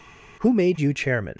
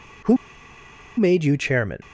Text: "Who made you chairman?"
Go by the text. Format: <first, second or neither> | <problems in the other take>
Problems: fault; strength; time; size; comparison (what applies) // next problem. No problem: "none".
first | pauses between "Who" and "made"; noticeable; at 0.3 s; 0.80 s long